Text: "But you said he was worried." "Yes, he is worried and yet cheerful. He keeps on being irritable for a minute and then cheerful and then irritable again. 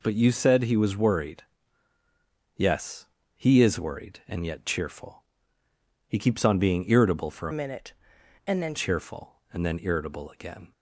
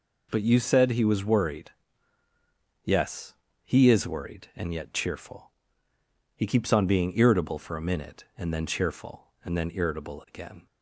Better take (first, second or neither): second